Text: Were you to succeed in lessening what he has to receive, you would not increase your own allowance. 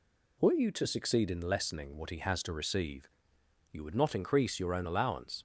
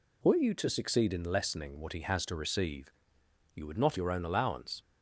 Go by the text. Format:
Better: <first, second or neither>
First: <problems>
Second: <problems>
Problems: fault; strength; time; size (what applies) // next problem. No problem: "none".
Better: first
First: none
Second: skips "increase"; at 3.9 s